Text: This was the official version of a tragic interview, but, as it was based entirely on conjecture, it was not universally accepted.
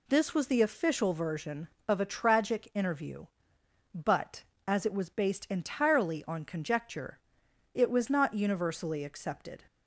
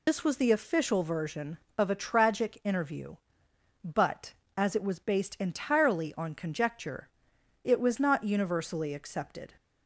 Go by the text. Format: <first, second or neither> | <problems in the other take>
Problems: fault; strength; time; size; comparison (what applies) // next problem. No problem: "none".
first | loses the start of "This"; at 0.0 s; 95 ms